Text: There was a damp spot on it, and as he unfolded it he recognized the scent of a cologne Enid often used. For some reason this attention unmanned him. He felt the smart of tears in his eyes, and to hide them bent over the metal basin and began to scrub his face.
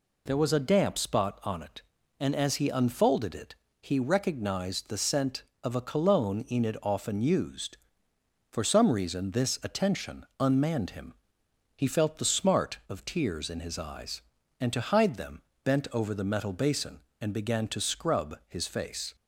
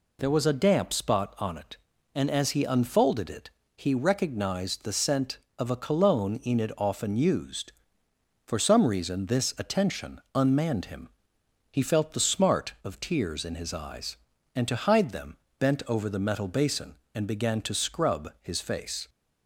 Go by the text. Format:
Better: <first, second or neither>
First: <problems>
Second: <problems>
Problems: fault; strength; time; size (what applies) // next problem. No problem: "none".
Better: neither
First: pauses between "it" and "he"; slight; at 3.5 s; 0.26 s long // pauses between "them" and "bent"; slight; at 15.4 s; 0.20 s long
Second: pauses between "it" and "he"; slight; at 3.4 s; 0.26 s long // pauses between "them" and "bent"; slight; at 15.3 s; 0.20 s long